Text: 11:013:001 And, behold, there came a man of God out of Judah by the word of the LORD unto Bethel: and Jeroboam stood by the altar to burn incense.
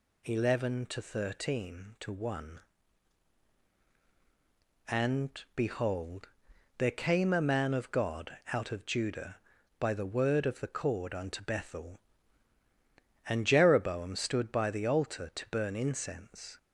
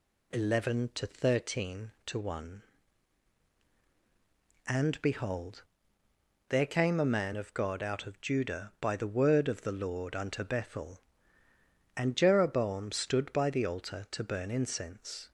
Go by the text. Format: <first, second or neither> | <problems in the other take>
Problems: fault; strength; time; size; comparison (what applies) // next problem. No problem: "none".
second | pauses between "God" and "out"; slight; at 8.3 s; 0.16 s long // says "Cord" for "LORD"; at 10.6 s